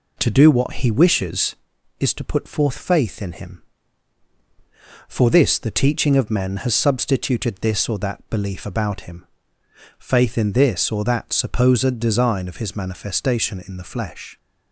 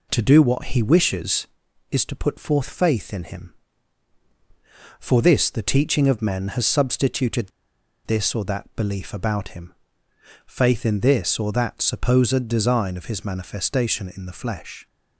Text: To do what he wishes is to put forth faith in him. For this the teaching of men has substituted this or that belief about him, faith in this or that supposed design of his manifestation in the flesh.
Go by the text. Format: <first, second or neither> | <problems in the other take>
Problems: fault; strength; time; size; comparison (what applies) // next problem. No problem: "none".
first | pauses between "substituted" and "this"; noticeable; at 7.4 s; 0.55 s long